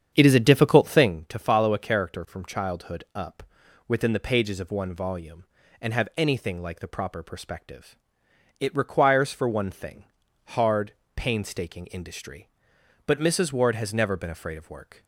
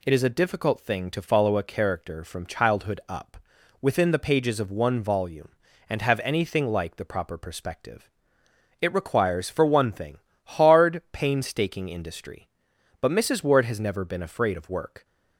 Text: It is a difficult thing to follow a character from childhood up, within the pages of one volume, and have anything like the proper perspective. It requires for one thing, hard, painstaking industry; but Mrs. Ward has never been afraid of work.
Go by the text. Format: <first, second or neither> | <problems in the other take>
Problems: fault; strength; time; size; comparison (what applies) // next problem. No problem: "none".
second | starts louder than the rest; strong; until 1.2 s; 8 dB